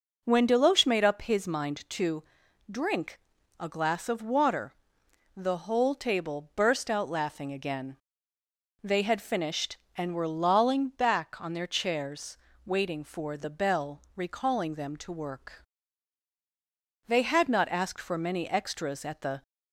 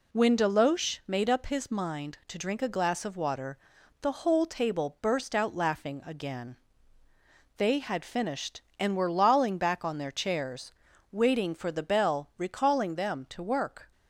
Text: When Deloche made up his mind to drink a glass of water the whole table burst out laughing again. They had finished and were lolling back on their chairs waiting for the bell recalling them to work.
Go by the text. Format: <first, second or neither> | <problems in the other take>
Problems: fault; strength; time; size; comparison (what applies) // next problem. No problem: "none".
second | pauses between "to" and "drink"; noticeable; at 2.2 s; 0.48 s long // pauses between "drink" and "a"; at 3.1 s; 0.40 s long // pauses between "water" and "the"; noticeable; at 4.7 s; 0.60 s long; also in the second // pauses between "chairs" and "waiting"; slight; at 12.3 s; 0.28 s long; also in the second // pauses between "bell" and "recalling"; slight; at 14.0 s; 0.15 s long // goes on to say "They had not asked for many extras at the"; strong; from 17.0 s on; 2.3 s long